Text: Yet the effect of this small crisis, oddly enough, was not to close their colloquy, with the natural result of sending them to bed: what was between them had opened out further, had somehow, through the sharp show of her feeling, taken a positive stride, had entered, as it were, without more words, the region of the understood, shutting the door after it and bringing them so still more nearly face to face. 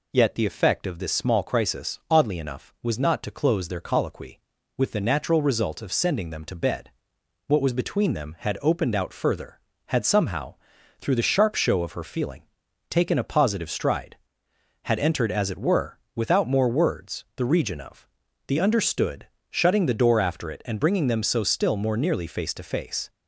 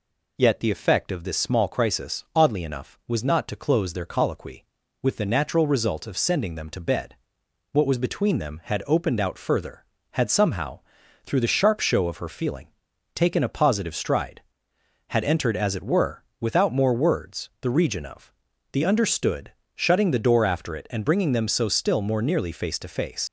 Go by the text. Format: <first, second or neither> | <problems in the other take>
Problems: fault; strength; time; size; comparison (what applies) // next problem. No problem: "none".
first | pauses between "of" and "the"; at 18.3 s; 0.40 s long; also in the first // leaves "face" unfinished; at 23.2 s; 70 ms